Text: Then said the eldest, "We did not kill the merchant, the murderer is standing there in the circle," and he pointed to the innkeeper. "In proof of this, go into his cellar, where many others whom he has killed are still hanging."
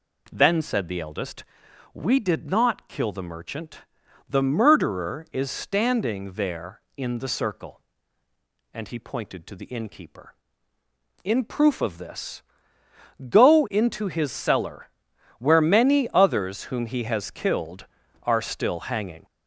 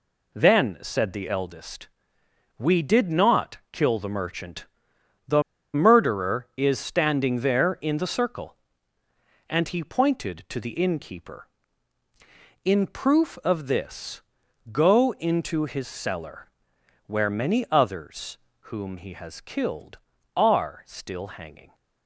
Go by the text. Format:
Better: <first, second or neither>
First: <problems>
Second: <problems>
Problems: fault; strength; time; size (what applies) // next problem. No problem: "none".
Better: first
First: none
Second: pauses between "the" and "murderer"; slight; at 5.4 s; 0.32 s long // pauses between "others" and "whom"; slight; at 18.3 s; 0.32 s long